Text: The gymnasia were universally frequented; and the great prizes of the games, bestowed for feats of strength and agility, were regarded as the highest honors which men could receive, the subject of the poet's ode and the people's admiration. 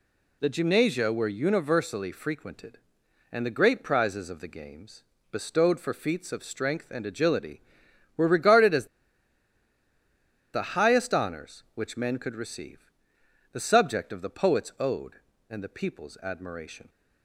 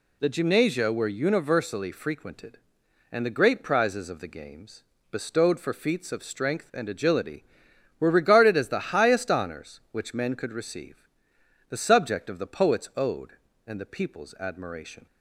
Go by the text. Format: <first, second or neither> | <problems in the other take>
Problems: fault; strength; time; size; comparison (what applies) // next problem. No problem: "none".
second | pauses between "as" and "the"; strong; at 8.8 s; 1.6 s long